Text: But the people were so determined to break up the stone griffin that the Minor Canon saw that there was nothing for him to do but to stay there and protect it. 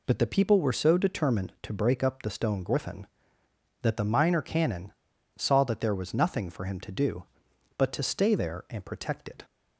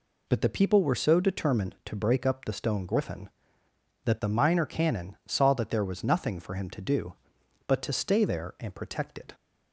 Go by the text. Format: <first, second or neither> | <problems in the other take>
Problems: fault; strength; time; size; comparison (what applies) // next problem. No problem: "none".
second | pauses between "Canon" and "saw"; at 4.9 s; 0.44 s long